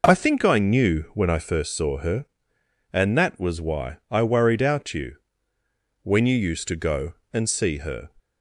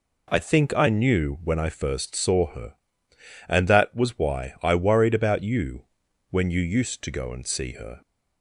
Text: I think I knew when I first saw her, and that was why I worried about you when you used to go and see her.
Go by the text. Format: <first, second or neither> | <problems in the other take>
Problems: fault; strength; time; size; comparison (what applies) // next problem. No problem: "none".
second | says "out" for "about"; at 4.6 s // pauses between "you" and "when"; noticeable; at 5.1 s; 0.88 s long; also in the second